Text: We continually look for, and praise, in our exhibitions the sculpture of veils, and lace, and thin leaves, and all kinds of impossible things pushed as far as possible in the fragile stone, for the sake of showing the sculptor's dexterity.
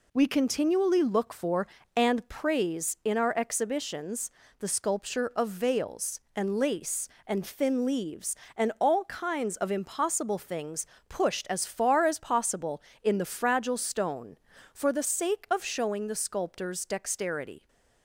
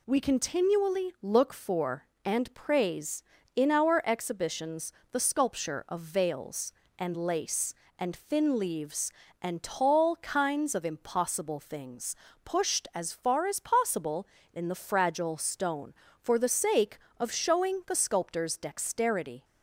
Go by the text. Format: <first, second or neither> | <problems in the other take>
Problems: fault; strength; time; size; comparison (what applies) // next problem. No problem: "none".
first | pauses between "exhibitions" and "the"; slight; at 4.9 s; 0.20 s long; slight in the first // says "tall" for "all"; at 9.6 s // pauses between "things" and "pushed"; slight; at 12.1 s; 0.28 s long; slight in the first